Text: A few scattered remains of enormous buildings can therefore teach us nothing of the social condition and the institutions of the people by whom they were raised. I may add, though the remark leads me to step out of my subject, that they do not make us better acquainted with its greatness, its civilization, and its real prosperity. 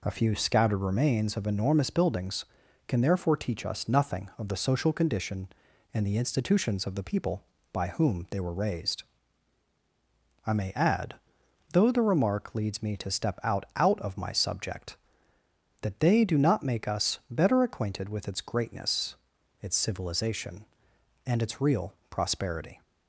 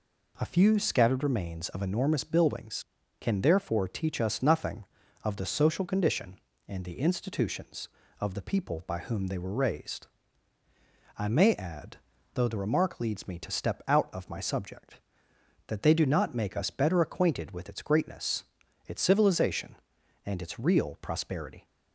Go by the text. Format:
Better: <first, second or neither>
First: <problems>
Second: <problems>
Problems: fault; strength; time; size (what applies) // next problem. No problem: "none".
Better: second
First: says "out" twice; at 13.7 s // pauses between "real" and "prosperity"; slight; at 21.9 s; 0.16 s long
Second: none